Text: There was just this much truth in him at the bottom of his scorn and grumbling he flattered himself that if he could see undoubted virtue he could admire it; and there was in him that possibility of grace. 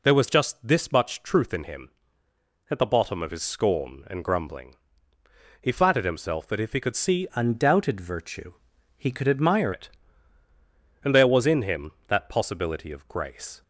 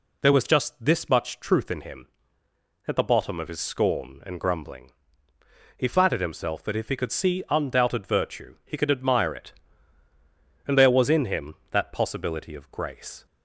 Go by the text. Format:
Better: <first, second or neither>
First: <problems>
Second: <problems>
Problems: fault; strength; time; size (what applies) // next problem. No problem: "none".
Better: second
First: pauses between "grumbling" and "he"; noticeable; at 4.7 s; 0.84 s long // changes voice from "undoubted" to "admire"; from 7.3 to 9.7 s; 2.4 s long // pauses between "virtue" and "he"; at 8.5 s; 0.44 s long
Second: pauses between "grumbling" and "he"; noticeable; at 4.9 s; 0.84 s long